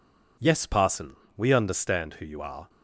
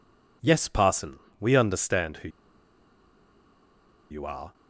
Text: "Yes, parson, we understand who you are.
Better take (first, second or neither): first